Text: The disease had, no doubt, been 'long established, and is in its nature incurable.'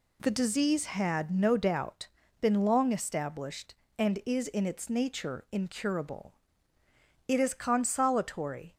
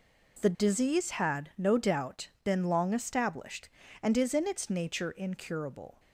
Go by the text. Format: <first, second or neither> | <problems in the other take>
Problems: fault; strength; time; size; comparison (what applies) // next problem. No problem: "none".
second | goes on to say "It is consolatory"; from 7.2 s on; 1.4 s long